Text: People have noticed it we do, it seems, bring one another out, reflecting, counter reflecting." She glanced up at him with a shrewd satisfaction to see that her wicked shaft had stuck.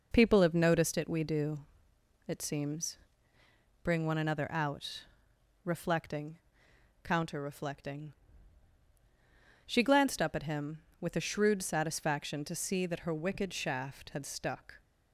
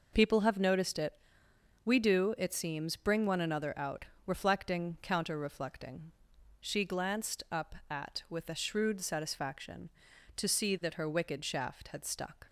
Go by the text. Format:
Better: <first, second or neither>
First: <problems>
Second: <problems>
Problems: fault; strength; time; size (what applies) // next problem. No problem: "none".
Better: first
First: none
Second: pauses between "it" and "we"; noticeable; at 1.1 s; 0.74 s long // skips "him"; at 8.2 s